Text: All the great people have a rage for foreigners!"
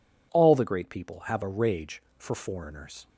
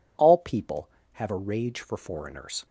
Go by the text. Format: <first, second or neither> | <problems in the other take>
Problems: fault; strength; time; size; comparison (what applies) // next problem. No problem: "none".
first | skips "the great"; at 0.3 s